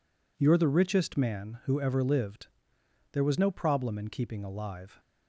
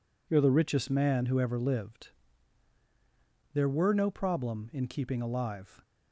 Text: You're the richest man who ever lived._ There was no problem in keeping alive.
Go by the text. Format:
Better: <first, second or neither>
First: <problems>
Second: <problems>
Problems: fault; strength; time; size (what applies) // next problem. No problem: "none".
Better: first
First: none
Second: says "were" for "was"; at 3.6 s